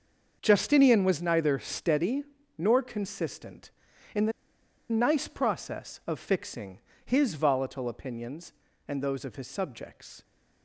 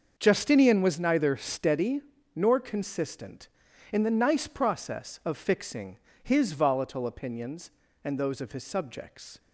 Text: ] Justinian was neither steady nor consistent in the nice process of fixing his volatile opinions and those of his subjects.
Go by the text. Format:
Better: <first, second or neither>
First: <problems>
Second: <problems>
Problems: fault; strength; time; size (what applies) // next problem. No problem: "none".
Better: second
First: starts louder than the rest; until 1.4 s; 6.5 dB // pauses between "steady" and "nor"; slight; at 2.2 s; 0.34 s long // pauses between "the" and "nice"; noticeable; at 4.3 s; 0.59 s long // pauses between "fixing" and "his"; slight; at 6.7 s; 0.26 s long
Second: starts louder than the rest; until 1.1 s; 6.5 dB // pauses between "steady" and "nor"; slight; at 2.0 s; 0.34 s long // pauses between "fixing" and "his"; slight; at 5.9 s; 0.26 s long